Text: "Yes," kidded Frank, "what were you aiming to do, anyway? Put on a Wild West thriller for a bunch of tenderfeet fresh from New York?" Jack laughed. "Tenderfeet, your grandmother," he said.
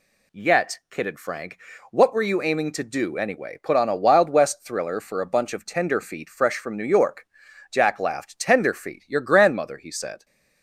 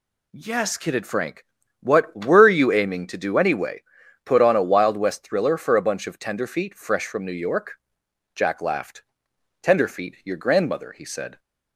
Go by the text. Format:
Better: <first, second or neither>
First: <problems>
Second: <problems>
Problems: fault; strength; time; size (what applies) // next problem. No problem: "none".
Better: second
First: says "Yet" for "Yes"; at 0.3 s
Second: none